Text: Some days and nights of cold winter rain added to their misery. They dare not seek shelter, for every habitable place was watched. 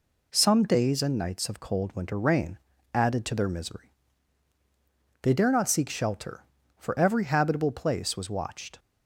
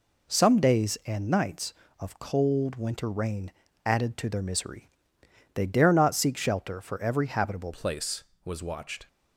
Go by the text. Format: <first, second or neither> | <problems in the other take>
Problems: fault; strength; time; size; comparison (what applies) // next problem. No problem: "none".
first | pauses between "rain" and "added"; slight; at 3.4 s; 0.36 s long; slight in the first // changes voice at "place"; from 7.7 s on; 1.3 s long